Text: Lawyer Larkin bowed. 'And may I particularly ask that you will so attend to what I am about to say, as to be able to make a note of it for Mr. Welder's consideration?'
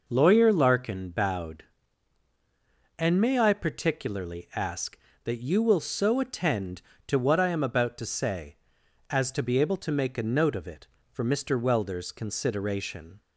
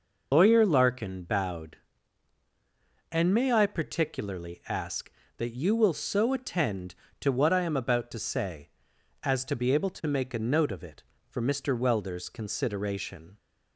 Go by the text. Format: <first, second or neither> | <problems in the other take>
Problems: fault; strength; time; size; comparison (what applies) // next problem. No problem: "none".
first | loses the start of "Lawyer"; at 0.3 s; 100 ms